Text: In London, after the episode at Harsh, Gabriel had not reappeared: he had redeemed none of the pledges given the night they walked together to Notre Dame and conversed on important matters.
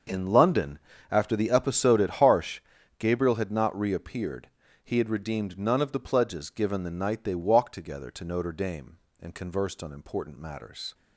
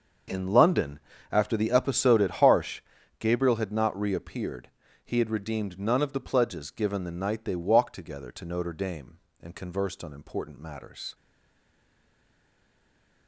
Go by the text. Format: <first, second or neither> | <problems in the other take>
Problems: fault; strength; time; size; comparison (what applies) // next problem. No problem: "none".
first | starts louder than the rest; until 1.6 s; 6.5 dB; also in the first // stays silent after the last word; from 11.1 s on; 2.1 s long